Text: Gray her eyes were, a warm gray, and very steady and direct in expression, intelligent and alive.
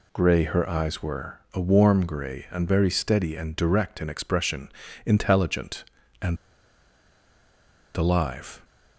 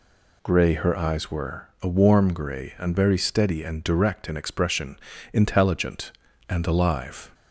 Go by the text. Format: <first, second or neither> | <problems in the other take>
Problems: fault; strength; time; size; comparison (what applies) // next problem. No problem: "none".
second | pauses between "and" and "alive"; strong; at 6.3 s; 1.6 s long